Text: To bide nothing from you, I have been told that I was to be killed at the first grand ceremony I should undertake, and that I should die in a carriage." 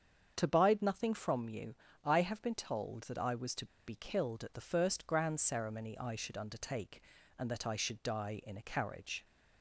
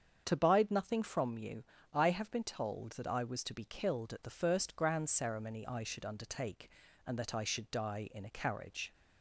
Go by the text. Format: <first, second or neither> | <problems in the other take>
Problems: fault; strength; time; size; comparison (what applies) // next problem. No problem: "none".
second | starts louder than the rest; strong; until 1.3 s; 7.5 dB; strong in the second // pauses between "to" and "be"; slight; at 3.6 s; 0.21 s long